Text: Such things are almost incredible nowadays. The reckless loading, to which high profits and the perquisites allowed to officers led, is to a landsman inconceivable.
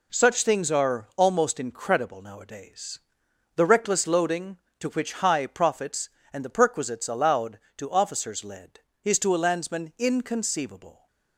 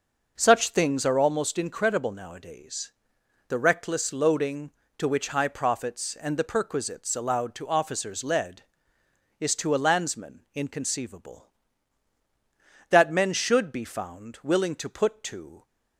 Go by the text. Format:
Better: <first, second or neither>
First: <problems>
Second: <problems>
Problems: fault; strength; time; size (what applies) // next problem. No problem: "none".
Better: first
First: none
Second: goes on to say "That men should be found willing to put to"; strong; from 12.9 s on; 2.7 s long